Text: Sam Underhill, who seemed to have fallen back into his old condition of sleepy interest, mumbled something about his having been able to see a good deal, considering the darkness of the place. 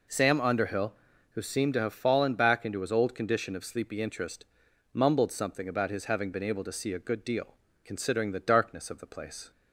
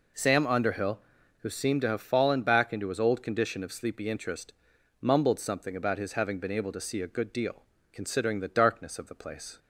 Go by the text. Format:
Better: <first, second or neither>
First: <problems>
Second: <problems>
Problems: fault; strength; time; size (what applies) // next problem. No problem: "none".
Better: neither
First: none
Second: none